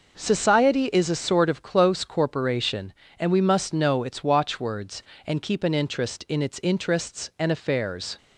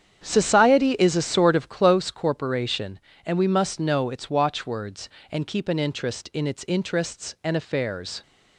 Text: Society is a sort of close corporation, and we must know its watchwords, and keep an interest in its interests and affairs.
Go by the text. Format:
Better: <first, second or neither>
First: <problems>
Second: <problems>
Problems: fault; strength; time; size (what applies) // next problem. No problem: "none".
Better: first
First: none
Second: starts louder than the rest; strong; until 2.1 s; 9 dB